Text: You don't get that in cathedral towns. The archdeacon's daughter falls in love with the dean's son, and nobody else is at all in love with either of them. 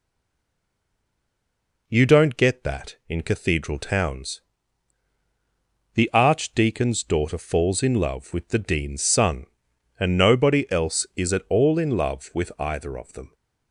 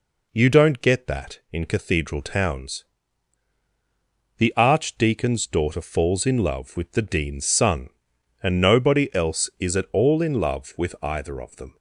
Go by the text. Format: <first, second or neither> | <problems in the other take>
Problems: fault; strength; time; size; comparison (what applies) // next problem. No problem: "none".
second | stays silent before the first word; noticeable; until 1.8 s; 1.8 s long